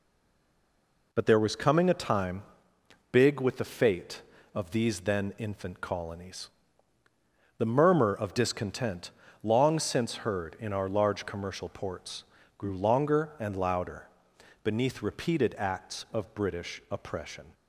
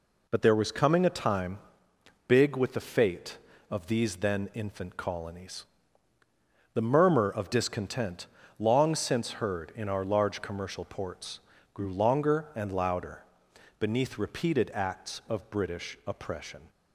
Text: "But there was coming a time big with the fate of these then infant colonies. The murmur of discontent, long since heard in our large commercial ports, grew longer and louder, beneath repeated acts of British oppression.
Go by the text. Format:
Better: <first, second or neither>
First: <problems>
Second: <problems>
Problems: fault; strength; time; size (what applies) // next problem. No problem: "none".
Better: second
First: stays silent before the first word; until 1.1 s; 1.1 s long // pauses between "time" and "big"; noticeable; at 2.4 s; 0.68 s long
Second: pauses between "time" and "big"; noticeable; at 1.5 s; 0.68 s long